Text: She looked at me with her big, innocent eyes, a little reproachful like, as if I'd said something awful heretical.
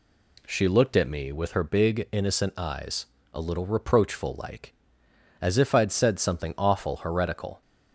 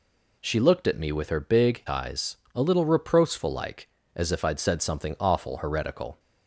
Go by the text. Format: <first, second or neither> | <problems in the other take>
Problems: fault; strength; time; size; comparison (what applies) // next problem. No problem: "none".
first | skips "innocent"; at 1.8 s